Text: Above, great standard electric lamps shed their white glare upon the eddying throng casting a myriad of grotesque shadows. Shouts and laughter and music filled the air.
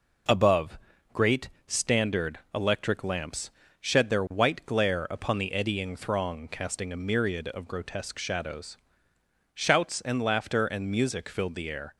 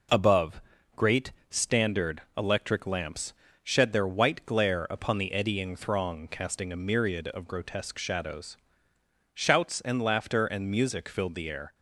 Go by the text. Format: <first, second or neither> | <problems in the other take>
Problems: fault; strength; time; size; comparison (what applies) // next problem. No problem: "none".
neither | pauses between "great" and "standard"; slight; the same in both // pauses between "lamps" and "shed"; slight; the same in both